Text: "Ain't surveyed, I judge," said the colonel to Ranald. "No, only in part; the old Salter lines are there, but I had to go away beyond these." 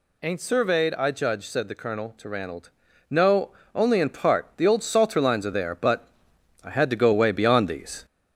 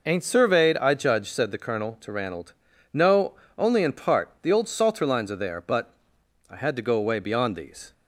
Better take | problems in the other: second | gets louder; slight; throughout; 2 dB // pauses between "but" and "I"; noticeable; at 6.0 s; 0.54 s long; noticeable in the second

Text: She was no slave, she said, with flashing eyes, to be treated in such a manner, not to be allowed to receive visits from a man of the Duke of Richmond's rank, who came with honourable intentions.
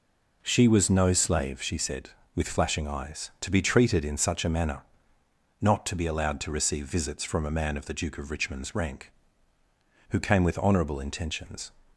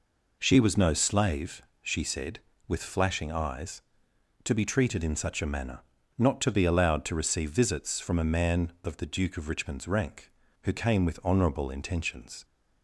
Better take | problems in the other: neither | none

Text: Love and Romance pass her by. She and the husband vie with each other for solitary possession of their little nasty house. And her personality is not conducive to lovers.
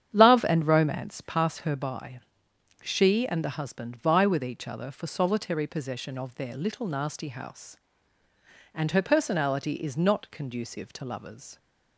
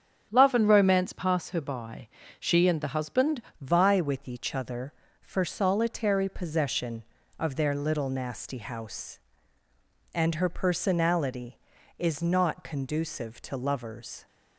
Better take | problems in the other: first | starts louder than the rest; strong; until 1.3 s; 8.5 dB; strong in the first // changes voice at "vie"; from 3.6 s on; 10.6 s long

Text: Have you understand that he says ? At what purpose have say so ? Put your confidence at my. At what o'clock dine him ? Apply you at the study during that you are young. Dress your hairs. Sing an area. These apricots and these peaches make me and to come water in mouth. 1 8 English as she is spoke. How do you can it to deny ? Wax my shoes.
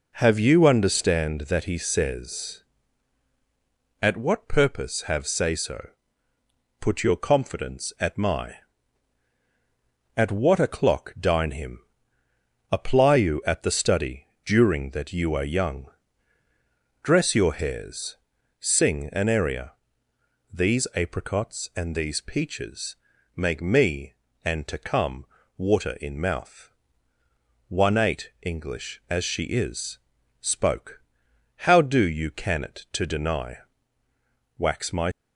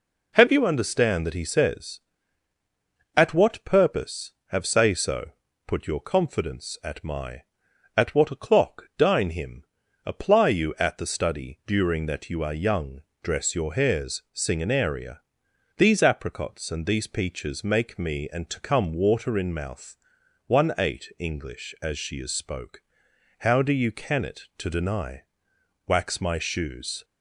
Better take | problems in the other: second | pauses between "study" and "during"; slight; at 14.2 s; 0.18 s long // pauses between "peaches" and "make"; at 22.9 s; 0.38 s long // pauses between "come" and "water"; slight; at 25.2 s; 0.32 s long // pauses between "is" and "spoke"; noticeable; at 29.9 s; 0.48 s long // stops before "shoes"; at 35.1 s

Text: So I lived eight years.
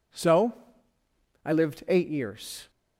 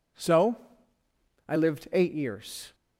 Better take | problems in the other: neither | pauses between "So" and "I"; noticeable; the same in both

